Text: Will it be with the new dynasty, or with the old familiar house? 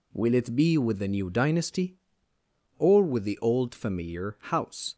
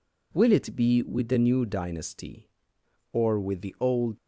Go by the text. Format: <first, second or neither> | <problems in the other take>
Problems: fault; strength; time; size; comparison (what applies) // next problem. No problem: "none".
first | stops before "familiar house"; at 4.1 s